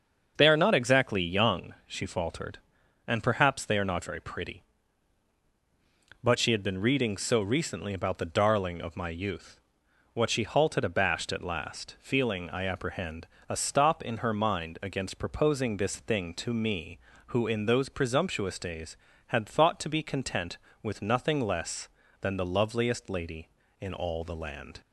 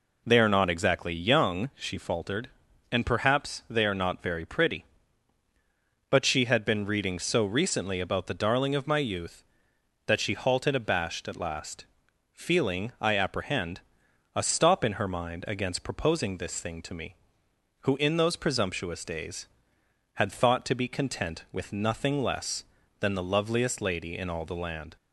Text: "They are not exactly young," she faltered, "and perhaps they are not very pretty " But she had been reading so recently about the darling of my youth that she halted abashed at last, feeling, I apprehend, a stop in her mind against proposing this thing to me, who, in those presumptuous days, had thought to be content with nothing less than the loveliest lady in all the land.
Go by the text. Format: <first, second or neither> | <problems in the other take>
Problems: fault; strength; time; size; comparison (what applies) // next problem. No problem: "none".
second | starts louder than the rest; strong; until 1.3 s; 8 dB // says "what" for "that"; at 10.1 s